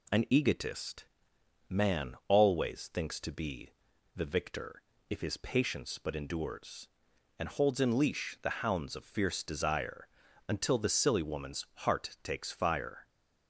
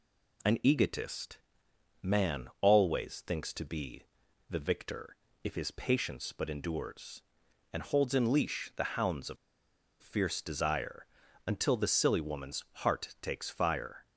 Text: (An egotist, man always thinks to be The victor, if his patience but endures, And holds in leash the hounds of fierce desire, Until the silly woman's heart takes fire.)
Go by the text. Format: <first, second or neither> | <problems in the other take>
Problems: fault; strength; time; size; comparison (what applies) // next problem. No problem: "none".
first | pauses between "be" and "The"; at 4.0 s; 0.44 s long; also in the first // pauses between "of" and "fierce"; noticeable; at 9.3 s; 0.64 s long